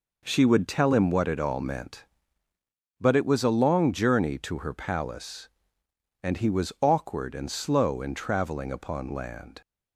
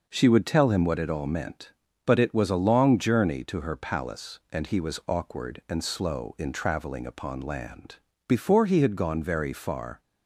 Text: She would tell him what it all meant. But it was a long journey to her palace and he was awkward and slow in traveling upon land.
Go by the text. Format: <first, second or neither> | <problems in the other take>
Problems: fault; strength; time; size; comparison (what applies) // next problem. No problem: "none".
first | goes on to say "Before he had gone very far"; strong; from 8.2 s on; 1.7 s long